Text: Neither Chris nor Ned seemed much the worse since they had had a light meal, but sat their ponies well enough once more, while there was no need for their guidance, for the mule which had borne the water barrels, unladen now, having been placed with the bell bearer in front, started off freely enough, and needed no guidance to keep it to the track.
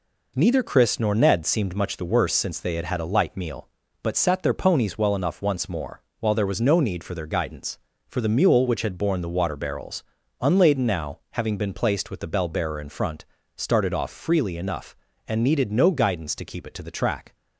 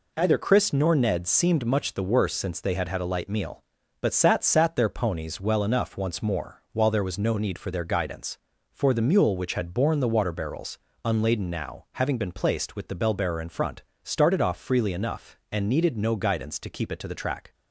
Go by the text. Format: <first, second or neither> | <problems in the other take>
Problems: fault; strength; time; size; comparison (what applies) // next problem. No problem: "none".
first | says "sat" twice; at 4.4 s